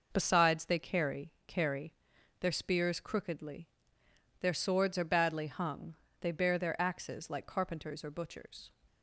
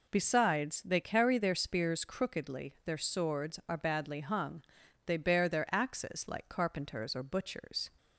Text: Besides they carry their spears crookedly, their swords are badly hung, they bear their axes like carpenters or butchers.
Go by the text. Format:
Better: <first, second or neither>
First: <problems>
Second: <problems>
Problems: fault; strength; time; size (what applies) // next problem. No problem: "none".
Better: second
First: says "carry" twice; at 1.4 s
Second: none